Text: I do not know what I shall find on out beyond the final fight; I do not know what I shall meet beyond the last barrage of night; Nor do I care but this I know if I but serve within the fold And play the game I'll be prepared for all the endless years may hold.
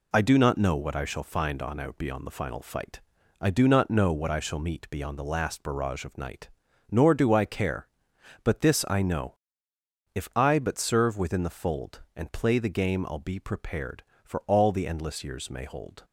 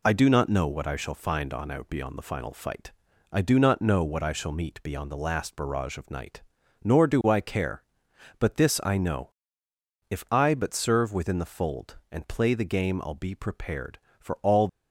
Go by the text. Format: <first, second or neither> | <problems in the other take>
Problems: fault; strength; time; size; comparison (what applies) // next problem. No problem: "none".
first | pauses between "know" and "if"; noticeable; at 9.3 s; 0.80 s long; noticeable in the first // stops before "the endless years may hold"; at 14.6 s